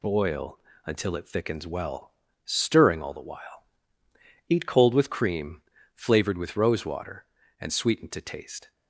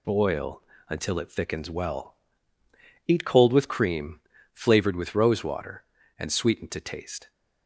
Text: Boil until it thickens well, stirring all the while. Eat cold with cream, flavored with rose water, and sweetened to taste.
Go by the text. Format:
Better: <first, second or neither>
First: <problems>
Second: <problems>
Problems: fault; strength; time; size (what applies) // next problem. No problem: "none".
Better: first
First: pauses between "Boil" and "until"; slight; at 0.5 s; 0.26 s long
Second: pauses between "Boil" and "until"; slight; at 0.6 s; 0.26 s long // skips "stirring all the while"; at 2.6 s